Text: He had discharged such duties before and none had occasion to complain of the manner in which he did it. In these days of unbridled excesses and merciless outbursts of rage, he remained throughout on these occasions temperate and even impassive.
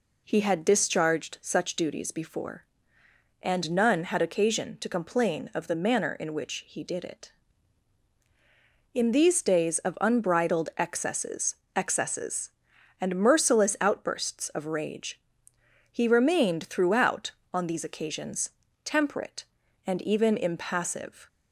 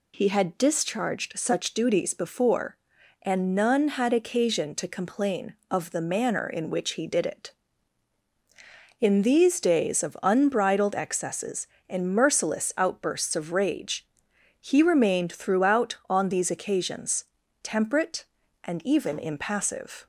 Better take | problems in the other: second | says "excesses" twice; at 11.7 s // pauses between "occasions" and "temperate"; slight; at 18.5 s; 0.34 s long; also in the second

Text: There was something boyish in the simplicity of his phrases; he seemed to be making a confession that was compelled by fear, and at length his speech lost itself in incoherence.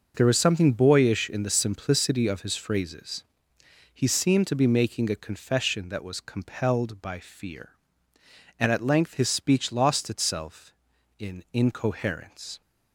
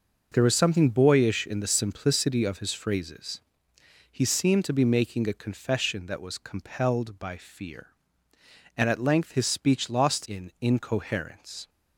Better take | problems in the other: first | skips "itself"; at 10.2 s

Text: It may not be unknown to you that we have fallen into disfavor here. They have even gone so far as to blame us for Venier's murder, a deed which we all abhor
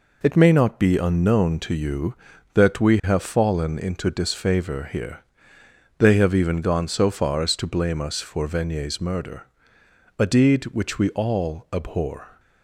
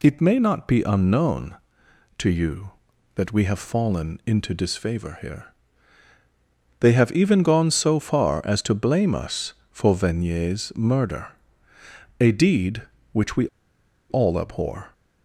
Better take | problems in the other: first | pauses between "we" and "all"; noticeable; at 13.4 s; 0.63 s long

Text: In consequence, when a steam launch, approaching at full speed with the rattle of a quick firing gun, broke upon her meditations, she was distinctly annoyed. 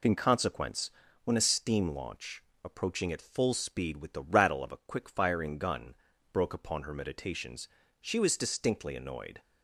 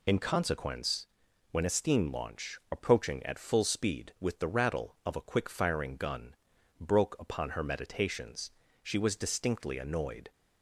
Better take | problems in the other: neither | none

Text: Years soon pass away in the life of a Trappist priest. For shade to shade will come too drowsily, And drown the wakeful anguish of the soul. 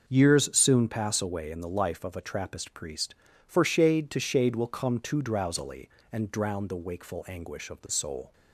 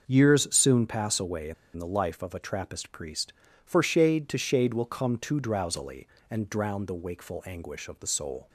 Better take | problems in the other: first | starts louder than the rest; noticeable; until 1.0 s; 6 dB; noticeable in the first // pauses between "in" and "the"; slight; at 1.5 s; 0.22 s long

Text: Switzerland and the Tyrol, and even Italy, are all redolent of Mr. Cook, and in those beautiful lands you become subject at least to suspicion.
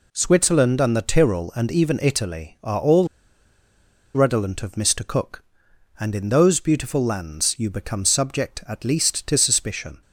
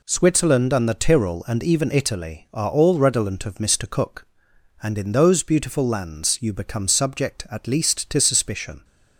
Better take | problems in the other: second | pauses between "all" and "redolent"; at 3.0 s; 1.0 s long

